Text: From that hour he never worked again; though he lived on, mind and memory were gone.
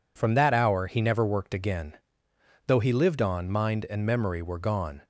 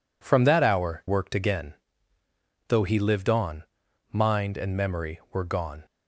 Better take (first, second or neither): first